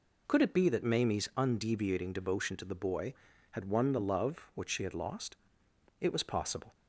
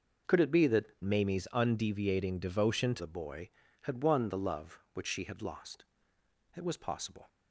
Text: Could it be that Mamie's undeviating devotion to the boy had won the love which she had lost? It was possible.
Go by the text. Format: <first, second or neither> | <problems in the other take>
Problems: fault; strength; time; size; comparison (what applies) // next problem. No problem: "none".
first | changes voice from "Mamie's" to "to"; from 1.0 to 3.0 s; 2.0 s long